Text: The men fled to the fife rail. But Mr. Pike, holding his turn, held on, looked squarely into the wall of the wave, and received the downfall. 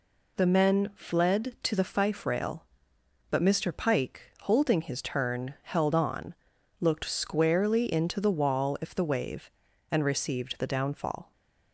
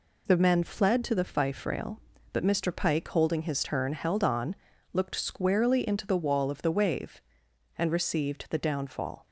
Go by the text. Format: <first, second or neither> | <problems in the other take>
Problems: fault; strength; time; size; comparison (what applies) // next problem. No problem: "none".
second | says "if" for "of"; at 8.8 s